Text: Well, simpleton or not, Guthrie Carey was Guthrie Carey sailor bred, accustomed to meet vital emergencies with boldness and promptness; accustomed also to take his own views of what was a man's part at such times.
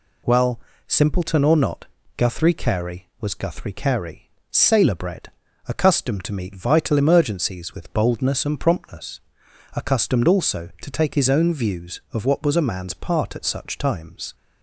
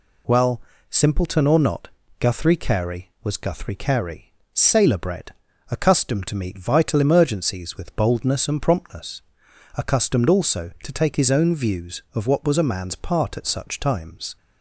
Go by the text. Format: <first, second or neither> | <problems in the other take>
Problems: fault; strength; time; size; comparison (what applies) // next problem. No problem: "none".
neither | pauses between "Carey" and "sailor"; slight; the same in both